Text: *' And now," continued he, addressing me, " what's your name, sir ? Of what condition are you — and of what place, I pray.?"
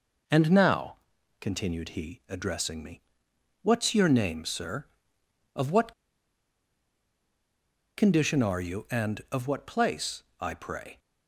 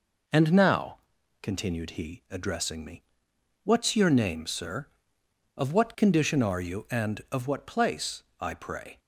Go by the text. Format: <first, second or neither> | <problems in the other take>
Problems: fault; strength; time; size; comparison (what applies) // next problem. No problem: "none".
second | pauses between "what" and "condition"; strong; at 5.9 s; 2.0 s long